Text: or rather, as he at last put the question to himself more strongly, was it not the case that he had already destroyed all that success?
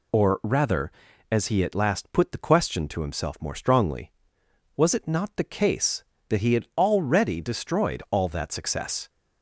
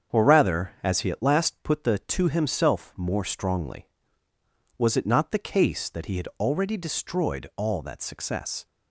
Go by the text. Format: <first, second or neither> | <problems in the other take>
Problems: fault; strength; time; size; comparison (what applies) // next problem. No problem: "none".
first | starts louder than the rest; strong; until 1.2 s; 7.5 dB // skips "question"; at 1.9 s